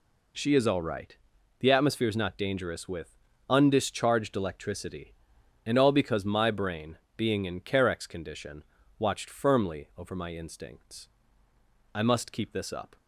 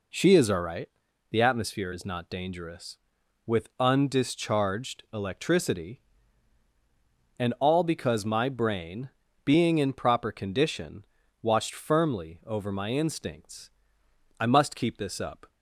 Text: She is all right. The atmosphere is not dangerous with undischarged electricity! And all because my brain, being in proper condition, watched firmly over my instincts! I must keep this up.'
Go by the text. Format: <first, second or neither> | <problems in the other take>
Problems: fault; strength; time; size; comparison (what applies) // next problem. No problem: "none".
second | pauses between "with" and "undischarged"; slight; at 3.1 s; 0.32 s long // says "carex" for "proper"; at 7.6 s